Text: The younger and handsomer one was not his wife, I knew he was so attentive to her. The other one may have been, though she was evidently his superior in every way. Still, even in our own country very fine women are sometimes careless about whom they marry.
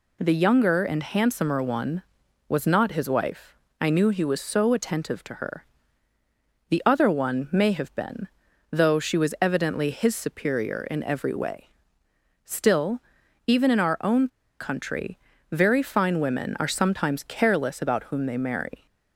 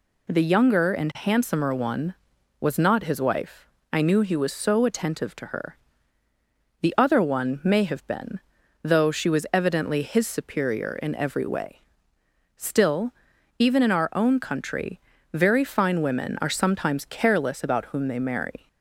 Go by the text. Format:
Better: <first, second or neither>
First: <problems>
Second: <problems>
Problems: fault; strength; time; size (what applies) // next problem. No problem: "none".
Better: second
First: pauses between "own" and "country"; slight; at 14.2 s; 0.32 s long // pauses between "country" and "very"; slight; at 15.1 s; 0.32 s long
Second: pauses between "country" and "very"; slight; at 15.0 s; 0.32 s long